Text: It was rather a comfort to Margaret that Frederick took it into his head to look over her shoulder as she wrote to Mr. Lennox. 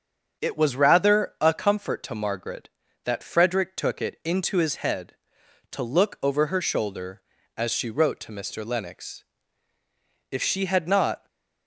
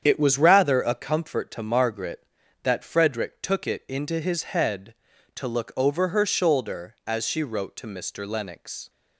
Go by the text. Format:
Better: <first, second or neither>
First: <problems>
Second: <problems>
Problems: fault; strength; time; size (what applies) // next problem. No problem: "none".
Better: second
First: starts louder than the rest; strong; until 1.4 s; 7.5 dB // goes on to say "If she had not"; noticeable; from 10.3 s on; 0.96 s long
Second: starts louder than the rest; strong; until 1.0 s; 8.5 dB